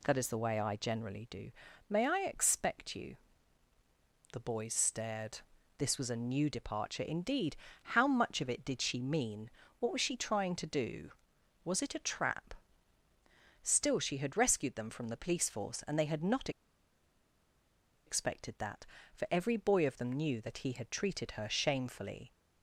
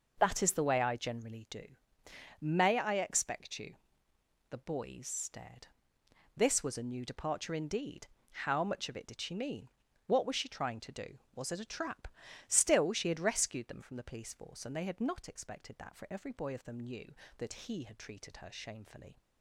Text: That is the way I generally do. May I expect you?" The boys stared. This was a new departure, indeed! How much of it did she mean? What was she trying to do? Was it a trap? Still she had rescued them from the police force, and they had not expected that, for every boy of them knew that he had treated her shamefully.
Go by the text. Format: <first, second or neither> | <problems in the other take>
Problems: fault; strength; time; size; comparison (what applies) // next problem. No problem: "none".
second | pauses between "not" and "expected"; strong; at 16.4 s; 1.5 s long